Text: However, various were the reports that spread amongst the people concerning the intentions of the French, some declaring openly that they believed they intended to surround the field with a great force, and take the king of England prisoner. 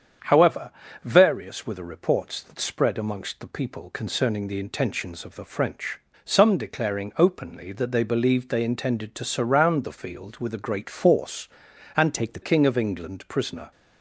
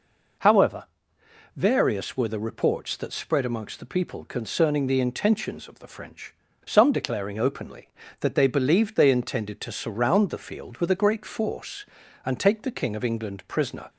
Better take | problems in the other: second | starts louder than the rest; strong; until 1.5 s; 7.5 dB // changes voice from "take" to "the"; from 12.1 to 12.4 s; 0.3 s long

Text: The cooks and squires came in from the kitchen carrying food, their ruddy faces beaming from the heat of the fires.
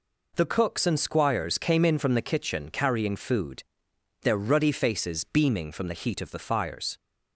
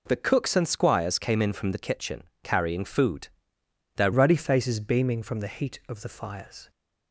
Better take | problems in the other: first | pauses between "kitchen" and "carrying"; slight; at 2.2 s; 0.22 s long // changes voice at "ruddy"; from 4.1 s on; 2.5 s long

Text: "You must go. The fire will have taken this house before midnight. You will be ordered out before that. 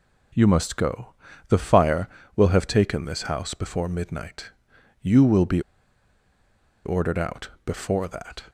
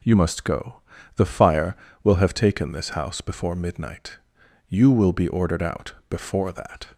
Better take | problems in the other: second | pauses between "be" and "ordered"; at 5.6 s; 1.2 s long // pauses between "out" and "before"; slight; at 7.4 s; 0.16 s long; slight in the second

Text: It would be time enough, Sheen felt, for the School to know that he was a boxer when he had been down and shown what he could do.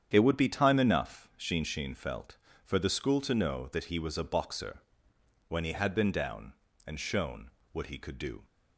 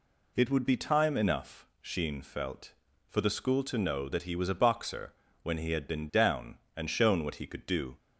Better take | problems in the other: second | starts louder than the rest; strong; until 1.1 s; 9 dB // says "Sheen" twice; at 1.6 s // pauses between "boxer" and "when"; noticeable; at 4.8 s; 0.66 s long; slight in the second // pauses between "shown" and "what"; slight; at 7.5 s; 0.20 s long

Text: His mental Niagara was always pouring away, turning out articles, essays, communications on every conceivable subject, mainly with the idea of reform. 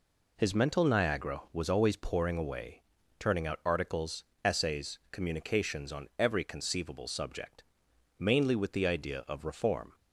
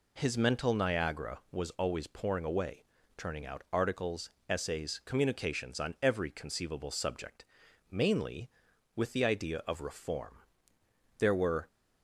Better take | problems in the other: first | goes on to say "There were"; slight; from 11.1 s on; 0.48 s long

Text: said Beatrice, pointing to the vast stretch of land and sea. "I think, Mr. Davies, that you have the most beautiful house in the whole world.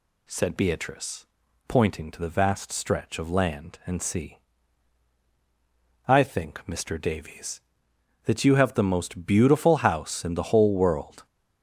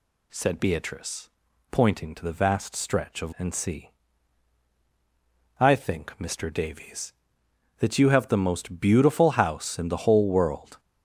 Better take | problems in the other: first | skips "land"; at 3.3 s

